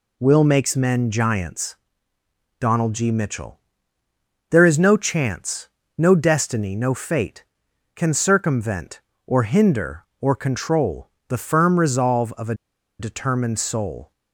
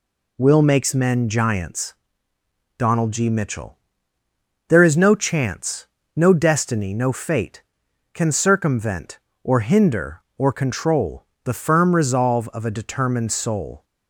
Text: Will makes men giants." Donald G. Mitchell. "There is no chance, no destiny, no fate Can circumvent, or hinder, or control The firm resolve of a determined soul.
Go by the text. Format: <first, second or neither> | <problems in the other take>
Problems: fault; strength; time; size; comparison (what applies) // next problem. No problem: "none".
second | pauses between "control" and "The"; slight; at 11.0 s; 0.18 s long; slight in the second // pauses between "a" and "determined"; at 12.5 s; 0.45 s long